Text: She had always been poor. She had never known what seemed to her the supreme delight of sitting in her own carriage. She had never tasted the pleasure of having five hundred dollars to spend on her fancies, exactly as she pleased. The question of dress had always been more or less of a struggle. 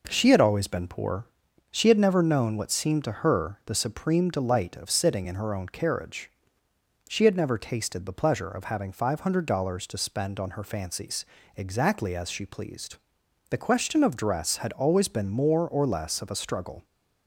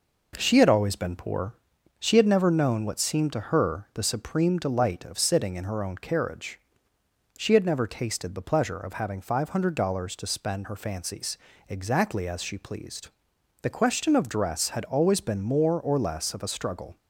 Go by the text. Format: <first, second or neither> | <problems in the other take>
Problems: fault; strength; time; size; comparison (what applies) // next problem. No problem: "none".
first | skips "on"; at 10.6 s